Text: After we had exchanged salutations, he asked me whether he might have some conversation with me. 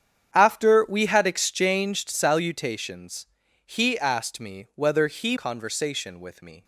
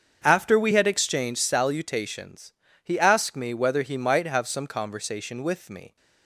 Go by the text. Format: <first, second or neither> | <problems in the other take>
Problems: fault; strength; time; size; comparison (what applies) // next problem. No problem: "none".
second | starts louder than the rest; strong; until 1.3 s; 8.5 dB; also in the second // skips "might have some"; at 5.3 s